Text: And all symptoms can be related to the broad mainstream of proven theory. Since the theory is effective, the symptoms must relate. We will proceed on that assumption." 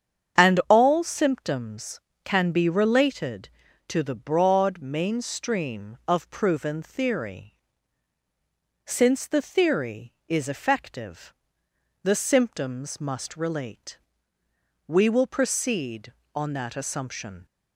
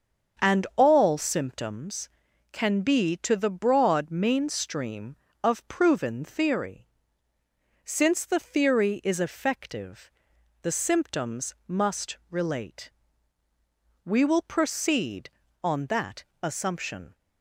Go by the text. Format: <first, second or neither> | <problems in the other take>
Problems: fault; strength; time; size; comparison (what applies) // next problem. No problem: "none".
first | starts louder than the rest; until 1.4 s; 7 dB; strong in the first // skips "related"; at 3.1 s // pauses between "that" and "assumption"; slight; at 16.2 s; 0.18 s long